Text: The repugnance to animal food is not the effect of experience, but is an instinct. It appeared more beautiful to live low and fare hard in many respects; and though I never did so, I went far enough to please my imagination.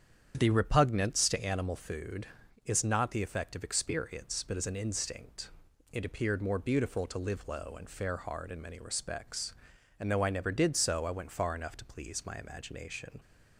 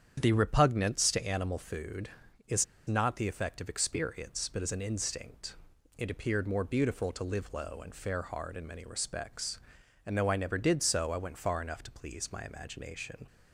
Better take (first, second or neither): first